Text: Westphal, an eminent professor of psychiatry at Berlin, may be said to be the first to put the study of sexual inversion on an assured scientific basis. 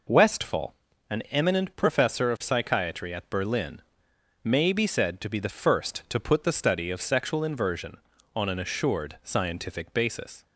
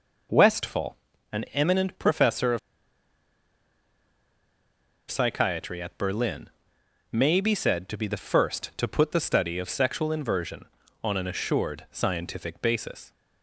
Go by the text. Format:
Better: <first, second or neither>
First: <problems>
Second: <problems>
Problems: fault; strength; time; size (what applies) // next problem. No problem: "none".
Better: first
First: none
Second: pauses between "of" and "psychiatry"; strong; at 2.5 s; 2.5 s long